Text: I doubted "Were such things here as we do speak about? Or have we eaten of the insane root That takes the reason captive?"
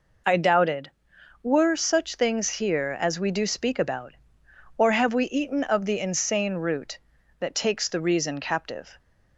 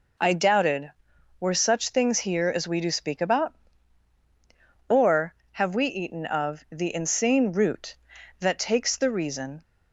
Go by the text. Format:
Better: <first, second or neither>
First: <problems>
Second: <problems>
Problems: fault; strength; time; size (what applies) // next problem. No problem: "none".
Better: first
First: none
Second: stops before "captive"; at 9.6 s